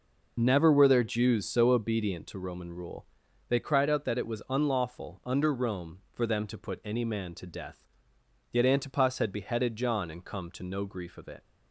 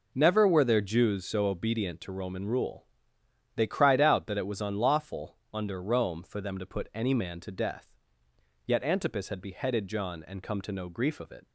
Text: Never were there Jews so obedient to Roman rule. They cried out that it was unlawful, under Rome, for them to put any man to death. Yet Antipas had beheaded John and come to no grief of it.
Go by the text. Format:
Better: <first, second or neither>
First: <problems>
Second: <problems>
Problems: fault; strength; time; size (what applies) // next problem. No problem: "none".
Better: neither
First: none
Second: none